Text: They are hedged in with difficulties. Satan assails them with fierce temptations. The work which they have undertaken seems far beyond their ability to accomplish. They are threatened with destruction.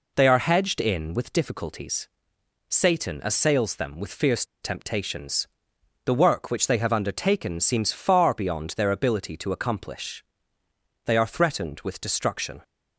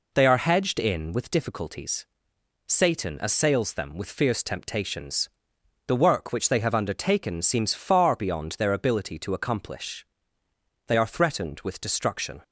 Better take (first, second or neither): second